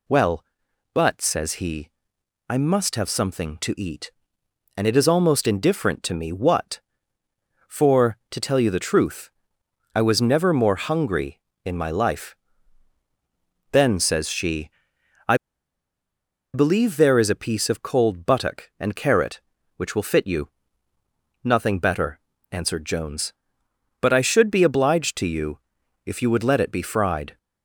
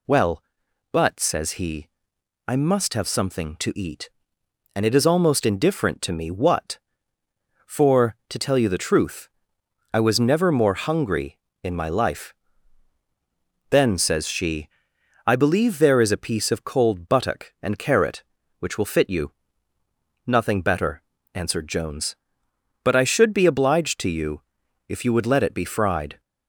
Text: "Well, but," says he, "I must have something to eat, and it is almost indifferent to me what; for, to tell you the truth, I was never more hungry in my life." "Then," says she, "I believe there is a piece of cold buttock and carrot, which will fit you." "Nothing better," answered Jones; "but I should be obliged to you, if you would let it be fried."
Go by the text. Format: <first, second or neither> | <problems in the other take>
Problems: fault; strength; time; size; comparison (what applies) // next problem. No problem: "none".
second | pauses between "I" and "believe"; at 15.3 s; 1.1 s long